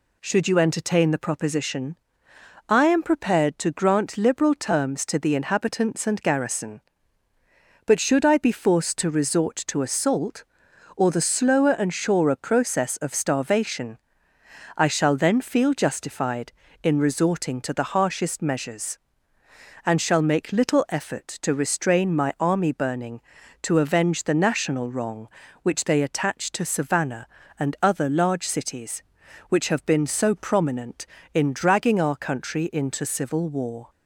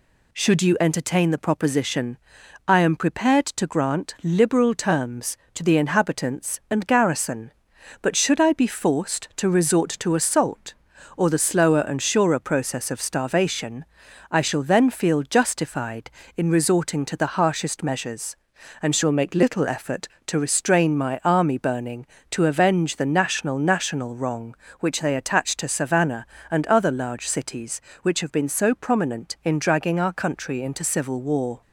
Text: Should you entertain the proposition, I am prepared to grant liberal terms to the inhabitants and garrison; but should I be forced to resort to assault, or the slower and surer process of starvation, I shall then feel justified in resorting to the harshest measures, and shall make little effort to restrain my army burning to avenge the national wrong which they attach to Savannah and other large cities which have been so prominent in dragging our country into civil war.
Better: first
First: none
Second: says "national" twice; at 23.5 s

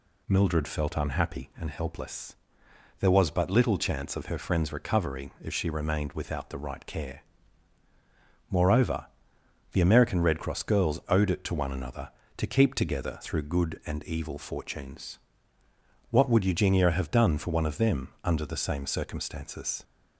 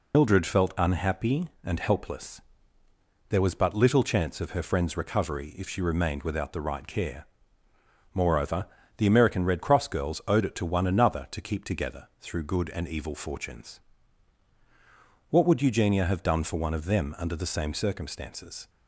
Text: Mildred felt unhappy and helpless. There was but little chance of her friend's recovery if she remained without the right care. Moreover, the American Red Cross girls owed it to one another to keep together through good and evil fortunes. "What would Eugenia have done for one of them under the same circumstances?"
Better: first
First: none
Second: loses the start of "Mildred"; at 0.1 s; 85 ms

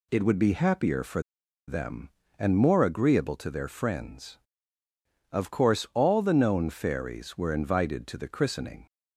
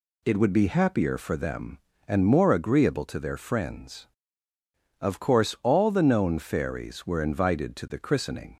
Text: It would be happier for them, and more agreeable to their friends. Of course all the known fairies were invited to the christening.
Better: second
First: pauses between "for" and "them"; noticeable; at 1.2 s; 0.47 s long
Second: none

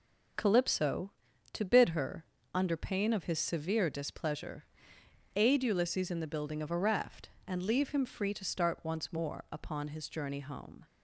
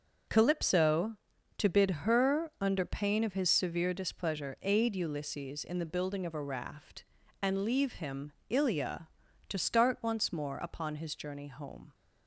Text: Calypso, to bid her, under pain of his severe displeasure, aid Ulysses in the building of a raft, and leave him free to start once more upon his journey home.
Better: first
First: none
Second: says "ilia" for "free"; at 8.4 s

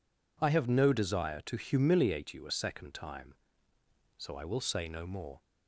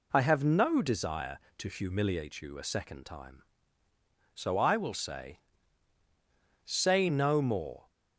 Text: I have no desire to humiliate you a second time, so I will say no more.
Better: first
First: none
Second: says "say" twice; at 6.6 s

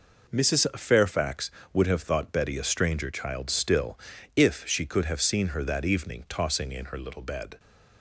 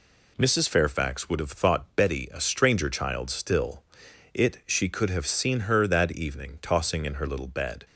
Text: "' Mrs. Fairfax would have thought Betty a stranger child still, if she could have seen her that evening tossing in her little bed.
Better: first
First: none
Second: says "it" for "if"; at 4.3 s

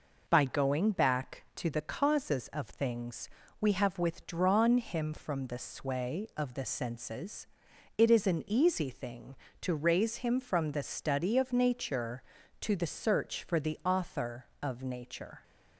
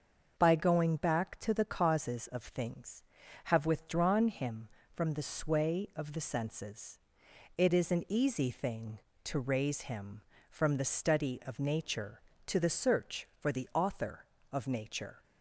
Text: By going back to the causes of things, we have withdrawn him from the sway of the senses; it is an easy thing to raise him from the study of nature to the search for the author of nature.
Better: first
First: none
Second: starts louder than the rest; until 1.3 s; 6.5 dB // skips "we"; at 3.2 s

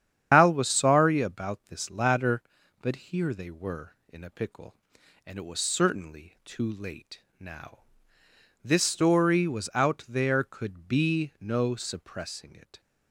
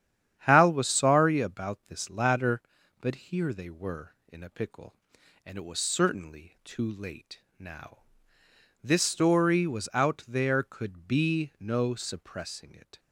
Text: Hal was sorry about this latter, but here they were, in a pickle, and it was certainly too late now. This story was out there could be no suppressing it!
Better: second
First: loses the start of "Hal"; at 0.3 s; 120 ms // starts louder than the rest; strong; until 1.3 s; 9 dB // pauses between "late" and "now"; slight; at 7.1 s; 0.20 s long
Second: starts louder than the rest; strong; until 1.4 s; 9.5 dB // pauses between "late" and "now"; slight; at 7.3 s; 0.20 s long

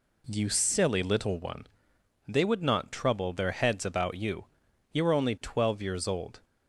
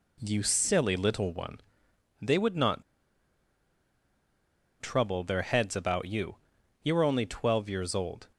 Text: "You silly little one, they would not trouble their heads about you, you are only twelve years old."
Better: first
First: none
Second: pauses between "not" and "trouble"; strong; at 2.8 s; 1.9 s long

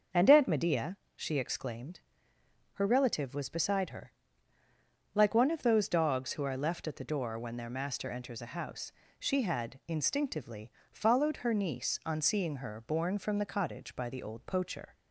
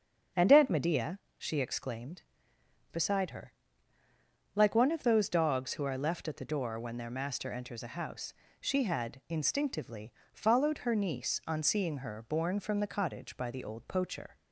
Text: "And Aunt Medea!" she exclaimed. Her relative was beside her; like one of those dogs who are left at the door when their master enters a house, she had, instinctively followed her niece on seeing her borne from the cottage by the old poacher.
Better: first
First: starts louder than the rest; noticeable; until 1.3 s; 6 dB // pauses between "instinctively" and "followed"; slight; at 10.7 s; 0.18 s long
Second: starts louder than the rest; until 1.5 s; 7 dB // skips "Her relative was"; at 2.5 s // pauses between "instinctively" and "followed"; slight; at 10.1 s; 0.18 s long

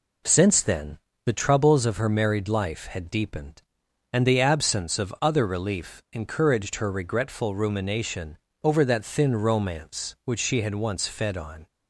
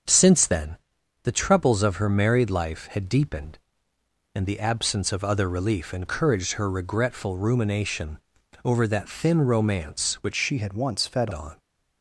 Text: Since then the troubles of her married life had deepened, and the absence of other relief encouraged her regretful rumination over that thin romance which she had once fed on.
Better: first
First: pauses between "then" and "the"; slight; at 0.9 s; 0.26 s long // pauses between "rumination" and "over"; slight; at 8.3 s; 0.24 s long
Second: starts louder than the rest; until 1.5 s; 6.5 dB // pauses between "then" and "the"; noticeable; at 0.7 s; 0.46 s long // pauses between "rumination" and "over"; at 8.1 s; 0.44 s long // changes voice from "she" to "fed"; from 10.3 to 11.3 s; 1.0 s long

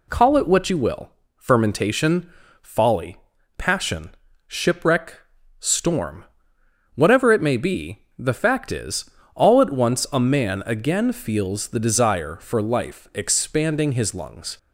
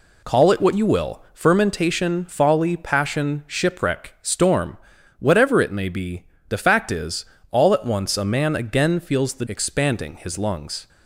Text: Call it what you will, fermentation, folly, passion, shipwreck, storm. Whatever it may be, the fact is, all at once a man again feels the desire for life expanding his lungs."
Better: first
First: none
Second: skips "desire for life"; at 9.4 s

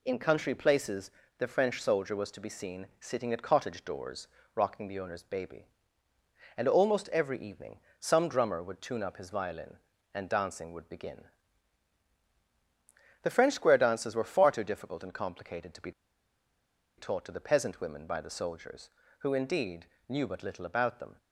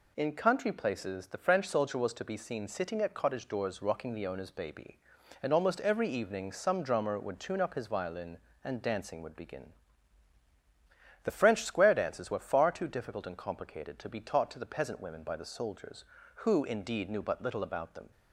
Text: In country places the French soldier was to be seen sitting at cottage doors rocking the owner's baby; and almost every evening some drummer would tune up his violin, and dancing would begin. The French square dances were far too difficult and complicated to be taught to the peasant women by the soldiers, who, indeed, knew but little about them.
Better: second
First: pauses between "places" and "the"; slight; at 1.1 s; 0.28 s long // pauses between "doors" and "rocking"; slight; at 4.2 s; 0.28 s long // pauses between "evening" and "some"; slight; at 7.8 s; 0.18 s long // pauses between "be" and "taught"; at 15.9 s; 1.0 s long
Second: none

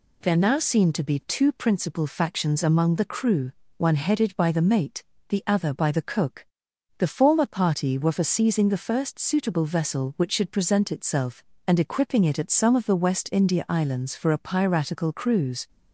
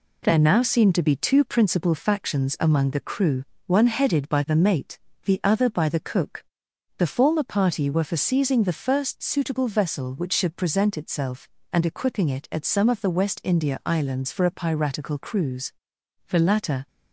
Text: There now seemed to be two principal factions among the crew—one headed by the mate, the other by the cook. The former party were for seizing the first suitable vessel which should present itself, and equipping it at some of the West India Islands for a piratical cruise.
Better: first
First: none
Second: goes on to say "The latter"; from 16.2 s on; 0.60 s long

